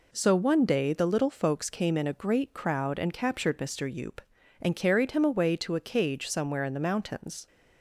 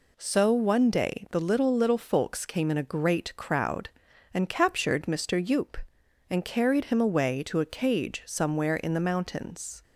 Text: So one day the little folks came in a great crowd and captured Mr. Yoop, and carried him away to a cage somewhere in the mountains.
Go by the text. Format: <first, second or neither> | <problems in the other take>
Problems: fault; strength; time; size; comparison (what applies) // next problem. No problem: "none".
first | says "little" twice; at 1.7 s